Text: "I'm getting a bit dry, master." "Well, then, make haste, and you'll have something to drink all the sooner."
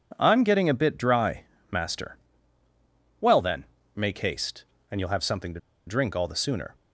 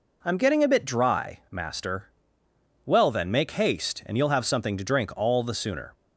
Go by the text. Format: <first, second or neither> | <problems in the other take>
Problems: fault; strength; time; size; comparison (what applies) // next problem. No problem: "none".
second | pauses between "to" and "drink"; slight; at 5.5 s; 0.26 s long